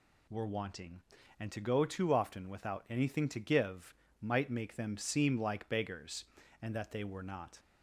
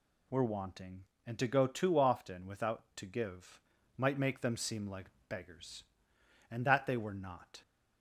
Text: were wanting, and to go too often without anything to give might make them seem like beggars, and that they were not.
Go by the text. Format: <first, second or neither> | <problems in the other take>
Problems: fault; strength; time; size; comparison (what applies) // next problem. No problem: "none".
first | skips "anything"; at 2.8 s // pauses between "give" and "might"; slight; at 3.6 s; 0.34 s long; slight in the first // pauses between "like" and "beggars"; slight; at 5.0 s; 0.18 s long